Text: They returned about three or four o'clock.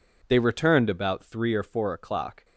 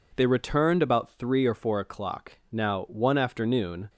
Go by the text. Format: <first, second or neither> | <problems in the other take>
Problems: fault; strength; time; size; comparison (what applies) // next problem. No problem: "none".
first | goes on to say "Now one afternoon"; from 2.5 s on; 1.3 s long